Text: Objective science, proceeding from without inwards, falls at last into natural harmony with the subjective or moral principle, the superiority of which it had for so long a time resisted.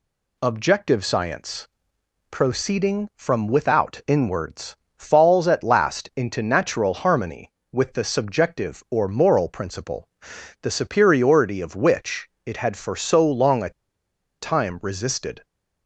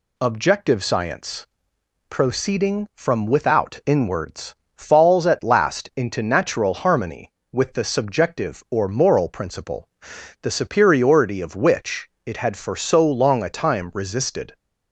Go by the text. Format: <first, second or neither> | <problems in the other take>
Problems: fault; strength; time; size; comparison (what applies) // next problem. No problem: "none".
second | pauses between "which" and "it"; slight; at 12.2 s; 0.16 s long; slight in the second // pauses between "a" and "time"; noticeable; at 13.6 s; 0.71 s long